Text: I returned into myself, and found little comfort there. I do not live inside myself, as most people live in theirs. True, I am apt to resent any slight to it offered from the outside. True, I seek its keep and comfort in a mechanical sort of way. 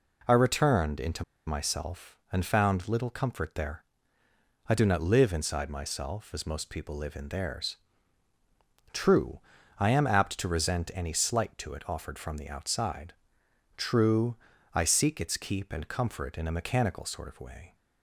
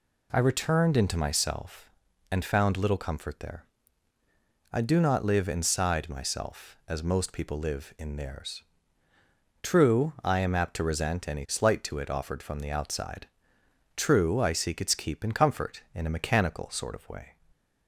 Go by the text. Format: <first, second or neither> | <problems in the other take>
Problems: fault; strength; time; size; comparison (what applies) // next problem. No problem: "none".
second | pauses between "into" and "myself"; slight; at 1.2 s; 0.22 s long